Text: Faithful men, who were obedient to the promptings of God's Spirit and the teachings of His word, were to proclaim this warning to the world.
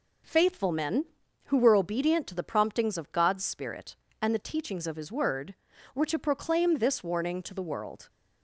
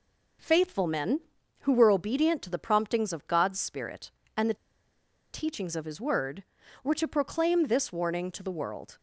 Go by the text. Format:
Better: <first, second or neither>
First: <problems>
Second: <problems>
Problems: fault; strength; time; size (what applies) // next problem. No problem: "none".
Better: first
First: none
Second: pauses between "the" and "teachings"; noticeable; at 4.5 s; 0.78 s long